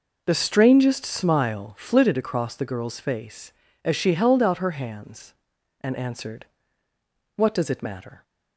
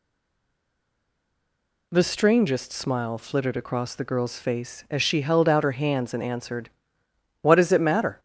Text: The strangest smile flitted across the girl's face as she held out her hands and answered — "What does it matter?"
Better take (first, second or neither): first